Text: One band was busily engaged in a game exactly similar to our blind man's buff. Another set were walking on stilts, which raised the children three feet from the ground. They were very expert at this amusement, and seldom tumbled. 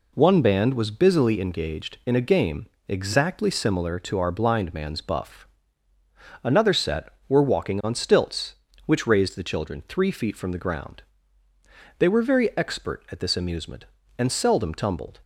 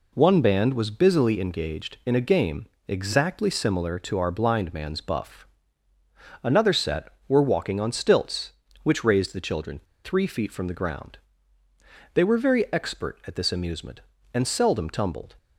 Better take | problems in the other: first | pauses between "game" and "exactly"; slight; at 2.6 s; 0.20 s long; slight in the first // pauses between "children" and "three"; slight; at 9.8 s; 0.24 s long

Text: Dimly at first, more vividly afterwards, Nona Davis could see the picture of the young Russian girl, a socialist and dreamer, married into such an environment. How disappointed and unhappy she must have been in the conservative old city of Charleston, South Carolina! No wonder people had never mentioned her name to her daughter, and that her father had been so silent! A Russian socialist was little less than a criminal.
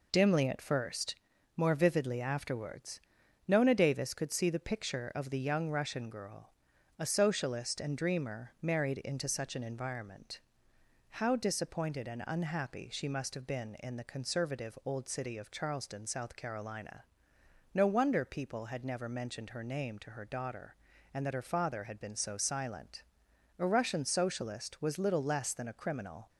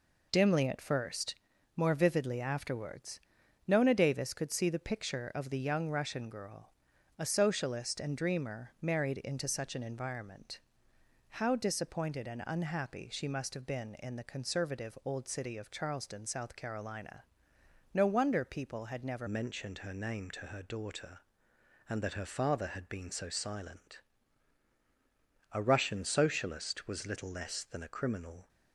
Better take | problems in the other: first | changes voice at "mentioned"; from 19.2 s on; 9.2 s long

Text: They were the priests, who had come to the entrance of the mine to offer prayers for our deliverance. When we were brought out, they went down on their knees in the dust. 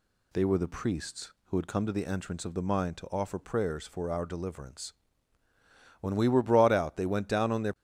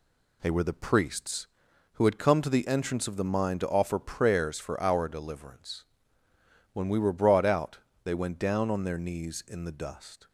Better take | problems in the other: second | stops before "knees in the dust"; at 7.7 s

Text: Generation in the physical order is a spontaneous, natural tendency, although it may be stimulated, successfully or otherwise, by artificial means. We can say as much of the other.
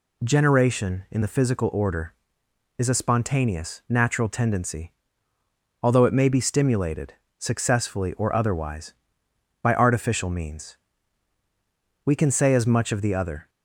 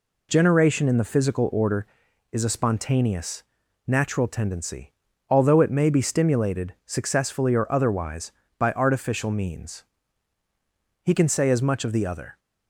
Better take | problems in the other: first | says "He" for "We"; at 11.0 s

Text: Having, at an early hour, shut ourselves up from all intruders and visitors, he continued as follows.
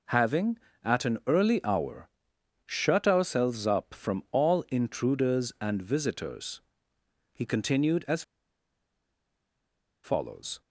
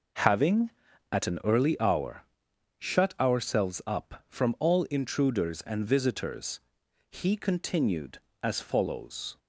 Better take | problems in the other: second | pauses between "as" and "follows"; strong; at 8.2 s; 1.8 s long

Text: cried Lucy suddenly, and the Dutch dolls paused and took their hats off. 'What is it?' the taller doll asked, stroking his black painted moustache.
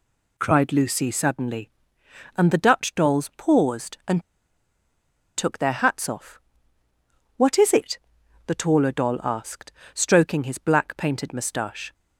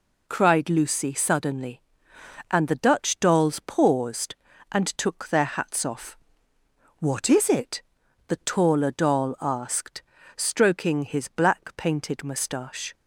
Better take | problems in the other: second | pauses between "and" and "took"; at 4.2 s; 1.1 s long

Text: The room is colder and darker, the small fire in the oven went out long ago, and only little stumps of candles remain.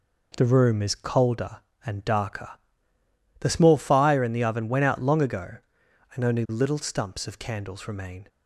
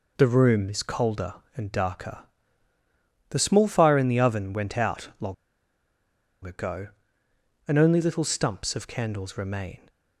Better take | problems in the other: first | pauses between "long" and "ago"; at 5.3 s; 1.1 s long

